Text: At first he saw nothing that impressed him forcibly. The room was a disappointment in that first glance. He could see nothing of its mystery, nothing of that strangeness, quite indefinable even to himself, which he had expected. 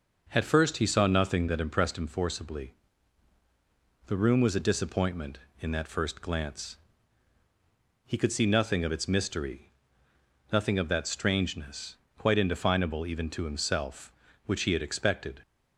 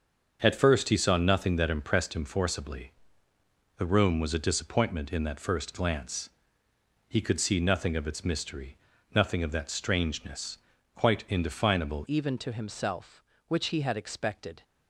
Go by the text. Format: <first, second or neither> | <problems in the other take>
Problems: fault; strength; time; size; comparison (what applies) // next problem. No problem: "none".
first | starts louder than the rest; until 1.4 s; 6.5 dB // changes voice at "even"; from 12.0 s on; 2.6 s long